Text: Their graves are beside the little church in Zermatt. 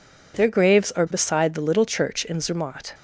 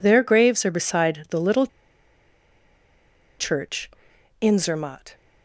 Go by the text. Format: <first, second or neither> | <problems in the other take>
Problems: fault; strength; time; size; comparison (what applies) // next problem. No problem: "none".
first | pauses between "little" and "church"; strong; at 1.6 s; 1.7 s long